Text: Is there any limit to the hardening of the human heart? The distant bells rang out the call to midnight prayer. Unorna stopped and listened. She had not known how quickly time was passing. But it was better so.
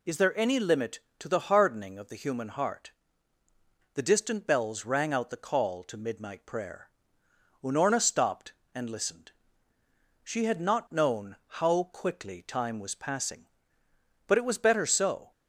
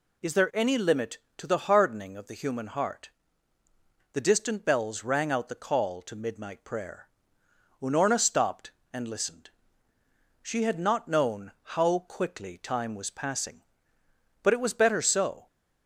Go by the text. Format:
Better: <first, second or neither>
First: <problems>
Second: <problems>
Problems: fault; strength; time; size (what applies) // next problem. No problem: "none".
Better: neither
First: none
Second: none